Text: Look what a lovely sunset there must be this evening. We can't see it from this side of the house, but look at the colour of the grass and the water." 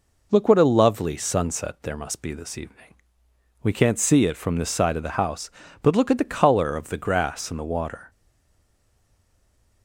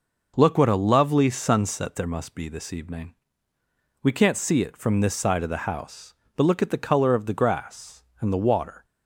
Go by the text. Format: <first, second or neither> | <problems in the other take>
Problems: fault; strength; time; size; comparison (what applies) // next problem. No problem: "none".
second | stays silent after the last word; noticeable; from 8.1 s on; 1.7 s long